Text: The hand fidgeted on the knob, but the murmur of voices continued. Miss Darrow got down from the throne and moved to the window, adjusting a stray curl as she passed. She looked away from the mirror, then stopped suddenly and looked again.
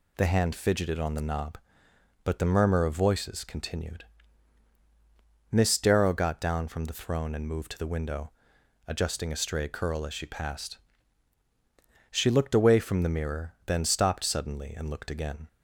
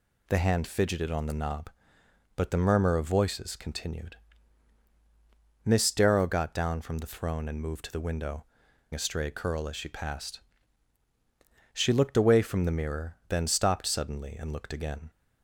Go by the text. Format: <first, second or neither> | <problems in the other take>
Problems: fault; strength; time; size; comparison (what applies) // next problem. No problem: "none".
first | skips "adjusting"; at 8.6 s